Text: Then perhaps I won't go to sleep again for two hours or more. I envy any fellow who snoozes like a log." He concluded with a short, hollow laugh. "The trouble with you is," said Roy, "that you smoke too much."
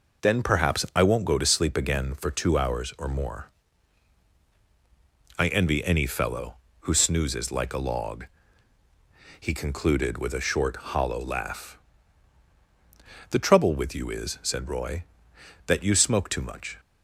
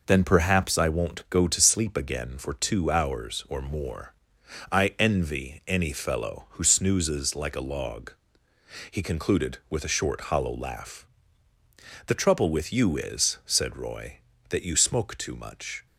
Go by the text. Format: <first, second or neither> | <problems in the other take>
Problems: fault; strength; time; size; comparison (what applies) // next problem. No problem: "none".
neither | none